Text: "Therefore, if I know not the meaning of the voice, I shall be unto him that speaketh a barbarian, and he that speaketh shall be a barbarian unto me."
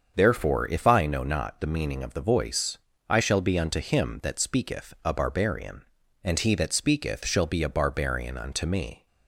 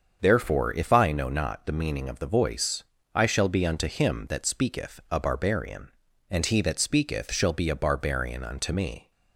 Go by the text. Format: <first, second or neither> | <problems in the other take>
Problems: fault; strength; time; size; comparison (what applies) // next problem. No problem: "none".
neither | starts louder than the rest; the same in both